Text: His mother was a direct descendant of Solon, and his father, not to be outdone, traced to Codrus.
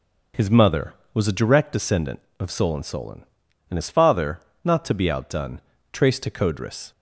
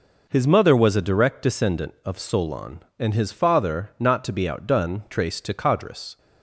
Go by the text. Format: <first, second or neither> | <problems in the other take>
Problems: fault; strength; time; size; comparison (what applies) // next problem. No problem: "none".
second | says "Solon" twice; at 2.8 s